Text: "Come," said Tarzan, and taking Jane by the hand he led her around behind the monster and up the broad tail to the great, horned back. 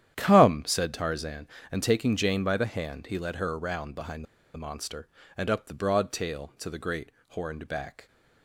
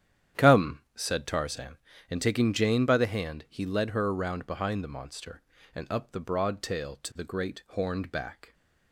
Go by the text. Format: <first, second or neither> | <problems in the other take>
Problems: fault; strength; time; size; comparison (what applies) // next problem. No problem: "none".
second | starts louder than the rest; strong; until 1.1 s; 10.5 dB; strong in the second // pauses between "behind" and "the"; slight; at 4.2 s; 0.29 s long